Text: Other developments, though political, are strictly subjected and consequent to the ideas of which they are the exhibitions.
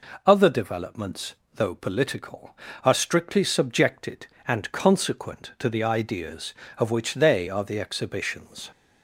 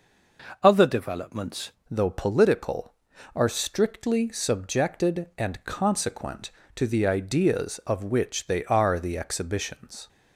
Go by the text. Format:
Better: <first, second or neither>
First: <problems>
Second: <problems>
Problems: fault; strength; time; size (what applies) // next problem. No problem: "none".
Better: first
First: none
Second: changes voice at "though"; from 1.8 s on; 8.2 s long